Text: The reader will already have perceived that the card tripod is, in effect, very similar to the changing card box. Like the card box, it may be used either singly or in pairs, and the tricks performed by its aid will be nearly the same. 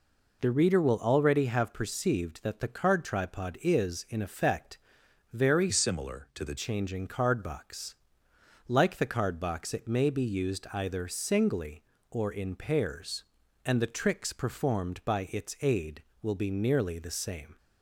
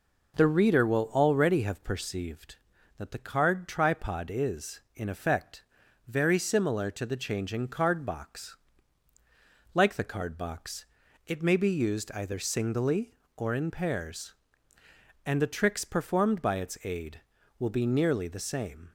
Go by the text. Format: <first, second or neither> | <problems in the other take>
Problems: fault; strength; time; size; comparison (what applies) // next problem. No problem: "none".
second | changes voice from "similar" to "the"; from 5.6 to 6.5 s; 0.9 s long